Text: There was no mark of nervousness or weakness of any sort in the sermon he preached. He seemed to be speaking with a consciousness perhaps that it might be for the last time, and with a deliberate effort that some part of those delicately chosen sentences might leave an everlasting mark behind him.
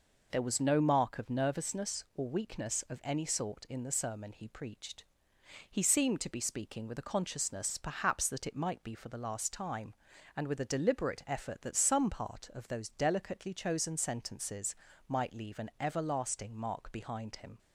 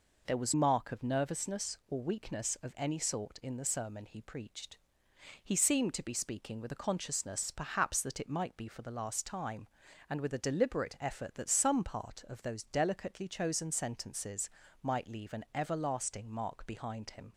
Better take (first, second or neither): first